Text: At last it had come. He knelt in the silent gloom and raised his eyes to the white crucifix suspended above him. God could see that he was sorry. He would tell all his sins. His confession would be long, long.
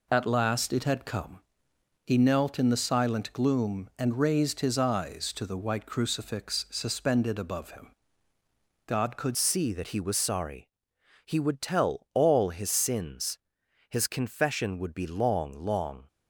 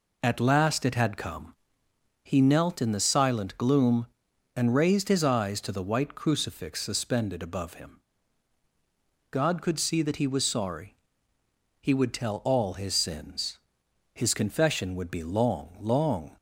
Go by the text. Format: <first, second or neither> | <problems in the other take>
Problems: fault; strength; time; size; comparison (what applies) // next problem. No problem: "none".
second | changes voice at "see"; from 9.3 s on; 6.7 s long